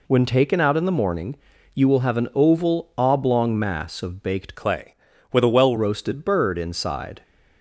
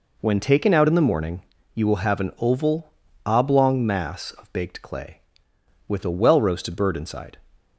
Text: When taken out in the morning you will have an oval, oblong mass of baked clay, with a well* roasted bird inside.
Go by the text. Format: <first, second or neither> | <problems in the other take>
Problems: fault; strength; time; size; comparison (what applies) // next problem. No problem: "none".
second | pauses between "morning" and "you"; at 1.3 s; 0.38 s long; slight in the second // changes voice from "clay" to "well"; from 4.5 to 5.7 s; 1.2 s long